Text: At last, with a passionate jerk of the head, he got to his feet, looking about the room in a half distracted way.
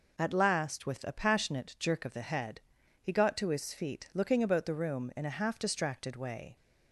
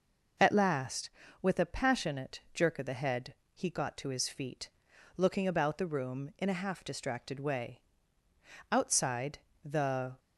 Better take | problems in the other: first | goes on to say "Outside the"; from 8.7 s on; 1.4 s long

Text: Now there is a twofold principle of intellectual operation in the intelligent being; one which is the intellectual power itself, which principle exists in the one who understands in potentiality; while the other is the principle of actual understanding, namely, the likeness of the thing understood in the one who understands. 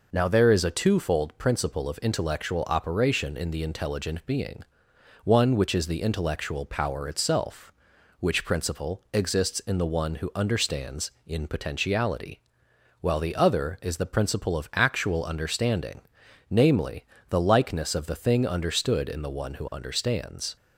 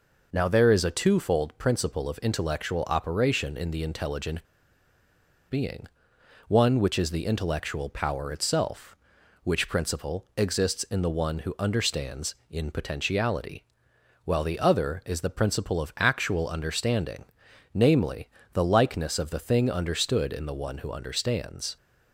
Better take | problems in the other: first | pauses between "intelligent" and "being"; at 4.4 s; 1.0 s long

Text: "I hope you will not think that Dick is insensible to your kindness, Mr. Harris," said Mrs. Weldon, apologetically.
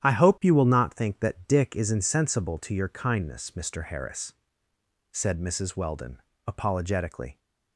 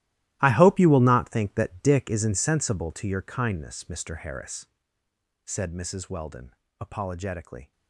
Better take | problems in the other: first | gets quieter; strong; throughout; 16.5 dB // starts louder than the rest; strong; until 1.4 s; 15.5 dB; strong in the first

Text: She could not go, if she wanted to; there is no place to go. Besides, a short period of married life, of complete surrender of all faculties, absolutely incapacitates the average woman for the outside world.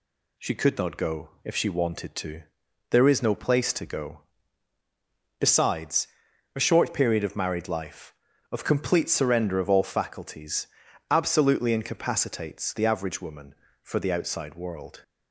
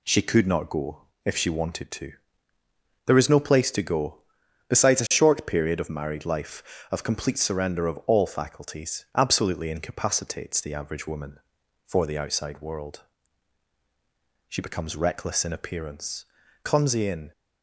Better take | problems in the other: first | goes on to say "She becomes reckless in appearance clumsy in"; strong; from 14.4 s on; 2.8 s long

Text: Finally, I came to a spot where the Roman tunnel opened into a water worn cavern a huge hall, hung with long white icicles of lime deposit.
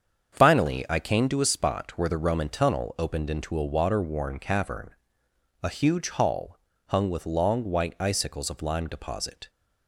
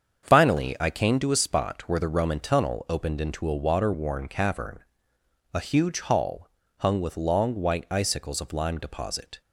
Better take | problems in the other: neither | starts louder than the rest; strong; the same in both // pauses between "cavern" and "a"; noticeable; the same in both

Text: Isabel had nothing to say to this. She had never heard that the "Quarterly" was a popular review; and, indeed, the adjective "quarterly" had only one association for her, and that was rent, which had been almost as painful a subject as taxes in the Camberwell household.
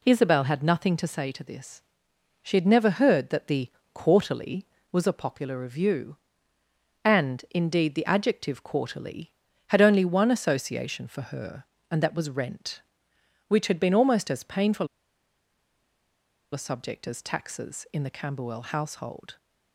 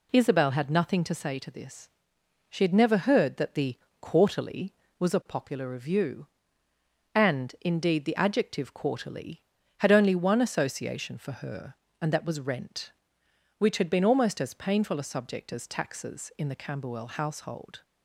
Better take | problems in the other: second | pauses between "the" and "Quarterly"; slight; at 3.7 s; 0.22 s long; slight in the second // pauses between "painful" and "a"; strong; at 14.8 s; 1.6 s long

